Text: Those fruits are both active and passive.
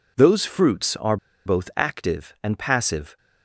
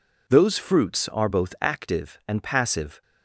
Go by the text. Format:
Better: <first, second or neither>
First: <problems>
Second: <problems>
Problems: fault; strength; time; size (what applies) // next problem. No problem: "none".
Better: second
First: pauses between "are" and "both"; slight; at 1.1 s; 0.29 s long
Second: none